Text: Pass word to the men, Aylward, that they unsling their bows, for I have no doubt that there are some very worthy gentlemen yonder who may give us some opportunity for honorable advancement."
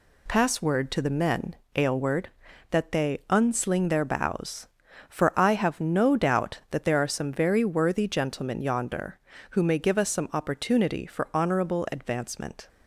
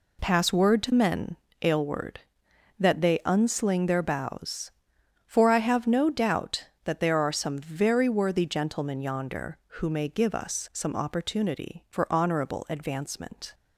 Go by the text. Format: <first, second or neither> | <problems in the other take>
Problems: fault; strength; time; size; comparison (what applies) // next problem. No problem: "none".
first | skips "the"; at 0.9 s